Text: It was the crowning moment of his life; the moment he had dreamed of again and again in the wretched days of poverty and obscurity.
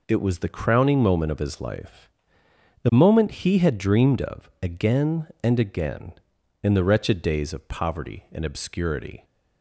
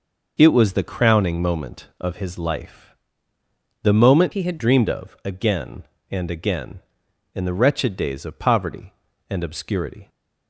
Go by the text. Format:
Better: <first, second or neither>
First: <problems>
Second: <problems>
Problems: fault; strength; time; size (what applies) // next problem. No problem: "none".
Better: first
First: none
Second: changes voice from "he" to "had"; from 4.3 to 4.5 s; 0.2 s long